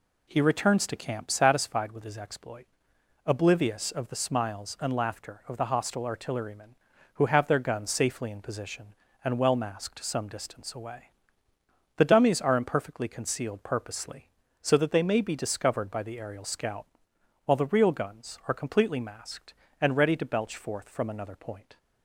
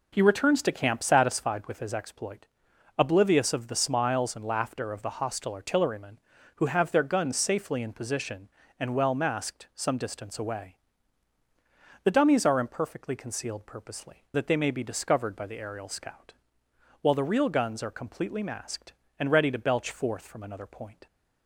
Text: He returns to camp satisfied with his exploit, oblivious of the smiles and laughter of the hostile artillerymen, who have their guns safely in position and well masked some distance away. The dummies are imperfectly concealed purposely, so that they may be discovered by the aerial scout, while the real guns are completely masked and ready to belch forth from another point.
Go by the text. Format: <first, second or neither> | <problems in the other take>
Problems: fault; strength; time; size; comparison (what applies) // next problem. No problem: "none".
first | skips "so"; at 14.2 s